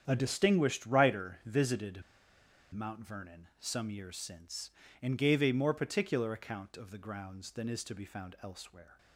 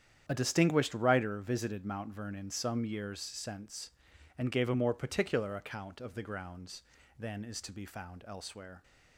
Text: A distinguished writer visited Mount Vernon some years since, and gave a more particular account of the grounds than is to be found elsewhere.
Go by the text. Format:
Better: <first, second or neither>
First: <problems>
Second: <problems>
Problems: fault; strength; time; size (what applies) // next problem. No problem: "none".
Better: second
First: starts louder than the rest; strong; until 1.0 s; 8.5 dB // pauses between "visited" and "Mount"; noticeable; at 2.0 s; 0.70 s long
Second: starts louder than the rest; strong; until 1.2 s; 9 dB